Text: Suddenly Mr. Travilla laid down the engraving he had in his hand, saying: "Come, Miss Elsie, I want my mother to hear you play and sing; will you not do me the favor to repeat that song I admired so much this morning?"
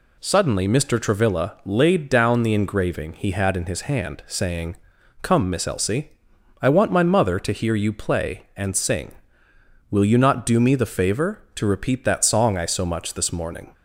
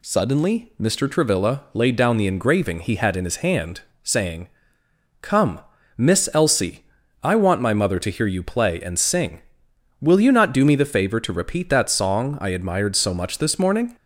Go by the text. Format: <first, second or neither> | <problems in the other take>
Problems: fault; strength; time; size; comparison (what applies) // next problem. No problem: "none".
second | skips "admired"; at 12.6 s